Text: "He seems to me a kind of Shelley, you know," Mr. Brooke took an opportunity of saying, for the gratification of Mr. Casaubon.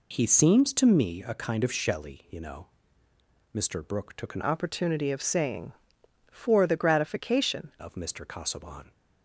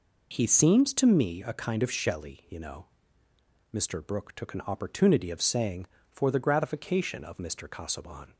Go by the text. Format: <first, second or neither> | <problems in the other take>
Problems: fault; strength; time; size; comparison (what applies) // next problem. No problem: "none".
second | changes voice from "opportunity" to "gratification"; from 4.4 to 7.7 s; 3.3 s long